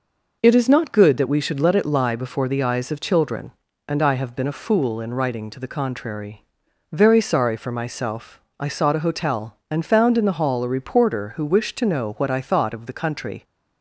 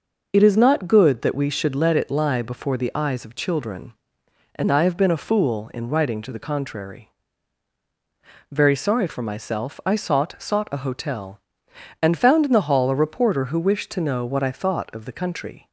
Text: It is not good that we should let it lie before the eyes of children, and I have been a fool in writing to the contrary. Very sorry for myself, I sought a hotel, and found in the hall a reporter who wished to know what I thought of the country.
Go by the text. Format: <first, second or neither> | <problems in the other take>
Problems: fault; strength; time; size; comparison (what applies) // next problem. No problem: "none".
first | says "sought" twice; at 10.3 s